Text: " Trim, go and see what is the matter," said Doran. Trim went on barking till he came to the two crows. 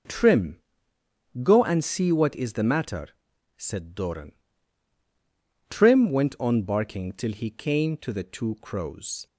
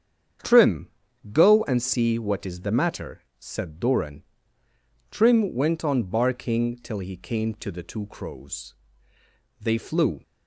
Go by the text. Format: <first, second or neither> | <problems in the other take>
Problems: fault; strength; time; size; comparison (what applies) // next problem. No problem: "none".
first | starts louder than the rest; strong; until 1.8 s; 8 dB // goes on to say "They flew"; noticeable; from 9.6 s on; 0.62 s long